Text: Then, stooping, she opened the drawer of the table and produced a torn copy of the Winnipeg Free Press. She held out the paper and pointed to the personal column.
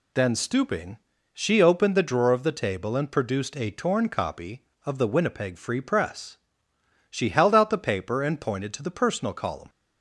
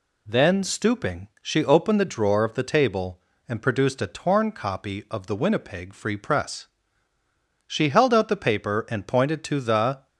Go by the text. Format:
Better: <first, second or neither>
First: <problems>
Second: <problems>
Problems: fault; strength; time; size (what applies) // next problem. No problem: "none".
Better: first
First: none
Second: stops before "personal column"; at 10.0 s